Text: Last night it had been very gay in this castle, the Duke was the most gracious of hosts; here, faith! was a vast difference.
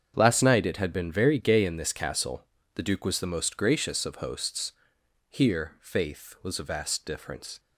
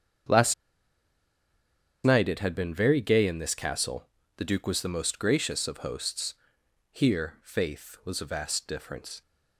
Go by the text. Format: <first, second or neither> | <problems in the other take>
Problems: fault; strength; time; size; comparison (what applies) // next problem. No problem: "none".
first | starts louder than the rest; strong; until 2.8 s; 7.5 dB; strong in the first // pauses between "Last" and "night"; strong; at 0.5 s; 1.5 s long